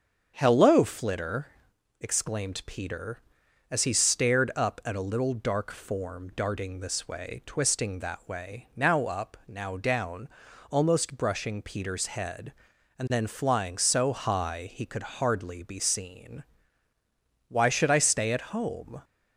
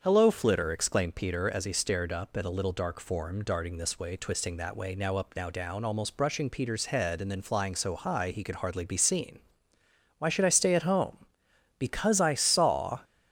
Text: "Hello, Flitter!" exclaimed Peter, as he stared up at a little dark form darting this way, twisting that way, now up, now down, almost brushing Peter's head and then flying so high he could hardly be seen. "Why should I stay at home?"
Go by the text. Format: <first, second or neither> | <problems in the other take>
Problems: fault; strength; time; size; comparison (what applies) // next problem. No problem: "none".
first | starts louder than the rest; strong; until 1.0 s; 7.5 dB; strong in the first // goes on to say "Because I saw"; noticeable; from 11.7 s on; 1.2 s long